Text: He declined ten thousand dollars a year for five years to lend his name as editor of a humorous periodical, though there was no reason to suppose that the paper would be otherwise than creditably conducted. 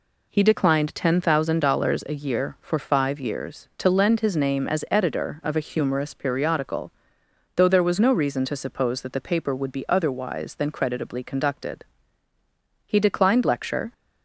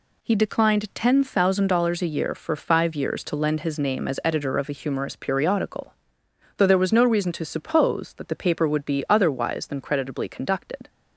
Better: second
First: goes on to say "He declined lecture"; noticeable; from 12.8 s on; 1.0 s long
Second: none

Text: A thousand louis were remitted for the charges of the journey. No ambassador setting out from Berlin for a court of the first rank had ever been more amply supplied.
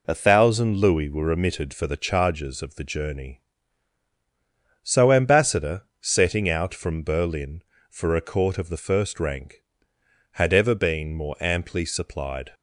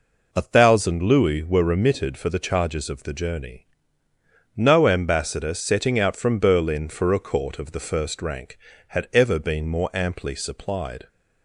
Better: second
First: says "So" for "No"; at 4.8 s // pauses between "ambassador" and "setting"; slight; at 5.8 s; 0.16 s long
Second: none

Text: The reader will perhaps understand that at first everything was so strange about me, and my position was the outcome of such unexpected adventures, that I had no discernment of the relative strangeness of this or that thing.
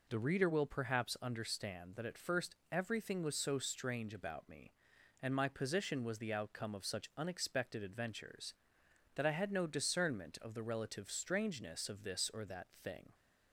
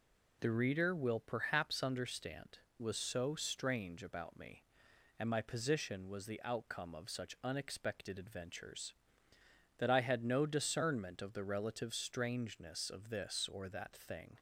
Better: first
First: none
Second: skips "that at first everything"; at 2.7 s

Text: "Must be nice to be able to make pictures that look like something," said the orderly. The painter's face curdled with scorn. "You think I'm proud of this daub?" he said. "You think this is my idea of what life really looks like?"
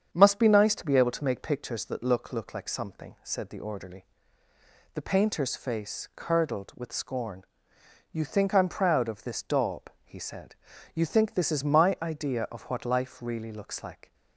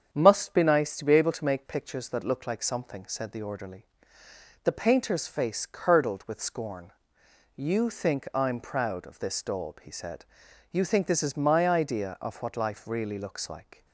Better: second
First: starts louder than the rest; strong; until 1.1 s; 8 dB // says "look" twice; at 2.3 s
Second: starts louder than the rest; strong; until 1.1 s; 7.5 dB

